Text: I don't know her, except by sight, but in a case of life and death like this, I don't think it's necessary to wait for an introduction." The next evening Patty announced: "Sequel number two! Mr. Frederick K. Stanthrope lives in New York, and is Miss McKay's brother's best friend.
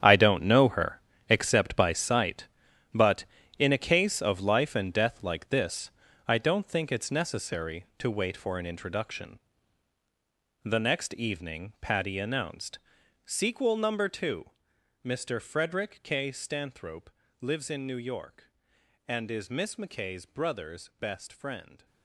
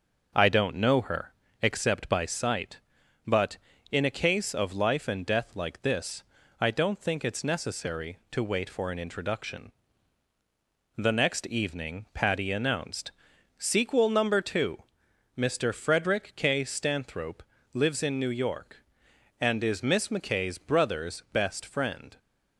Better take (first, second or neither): second